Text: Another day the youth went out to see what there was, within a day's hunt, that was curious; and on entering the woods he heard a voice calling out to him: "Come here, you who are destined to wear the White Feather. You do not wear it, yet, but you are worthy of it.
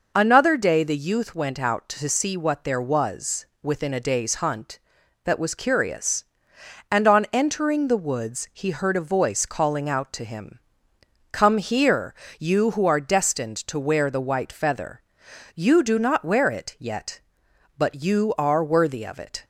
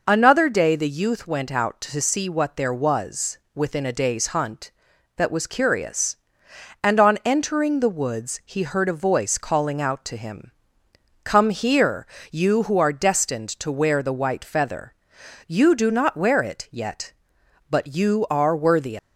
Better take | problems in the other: first | stops before "of it"; at 18.9 s

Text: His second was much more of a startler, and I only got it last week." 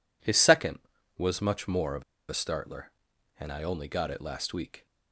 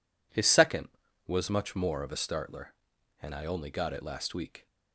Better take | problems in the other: second | pauses between "of" and "a"; slight; at 2.0 s; 0.25 s long

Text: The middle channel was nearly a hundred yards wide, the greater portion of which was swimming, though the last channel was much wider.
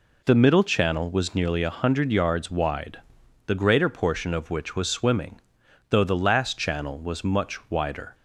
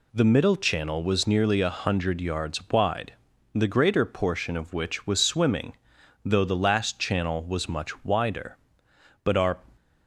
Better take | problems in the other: first | goes on to say "But our"; slight; from 9.2 s on; 0.38 s long

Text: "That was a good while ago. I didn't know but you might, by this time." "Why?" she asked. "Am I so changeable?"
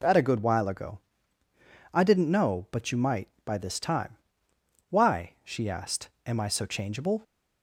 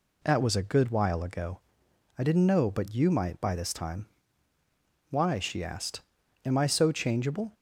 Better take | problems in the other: second | skips "was"; at 0.1 s

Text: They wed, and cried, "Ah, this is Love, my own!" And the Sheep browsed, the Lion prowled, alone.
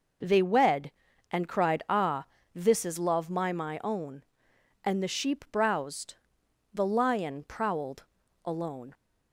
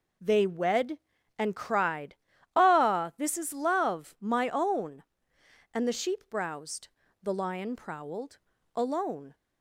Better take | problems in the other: second | says "my" twice; at 3.5 s

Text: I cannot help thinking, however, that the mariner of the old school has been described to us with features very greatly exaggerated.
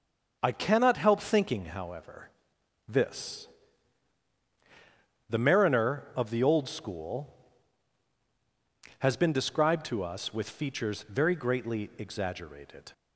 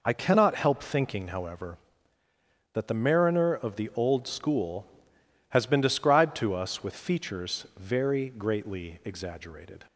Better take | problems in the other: second | starts louder than the rest; until 1.4 s; 6.5 dB // says "this" for "that"; at 2.8 s

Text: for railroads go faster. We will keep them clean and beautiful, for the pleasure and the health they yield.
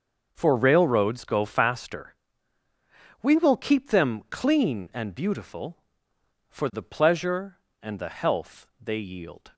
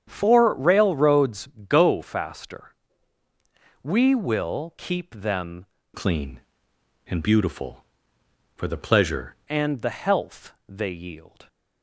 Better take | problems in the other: first | starts louder than the rest; strong; until 1.0 s; 8.5 dB; noticeable in the first // pauses between "railroads" and "go"; slight; at 1.4 s; 0.20 s long // changes voice from "clean" to "pleasure"; from 5.9 to 9.3 s; 3.4 s long // pauses between "health" and "they"; slight; at 10.5 s; 0.16 s long

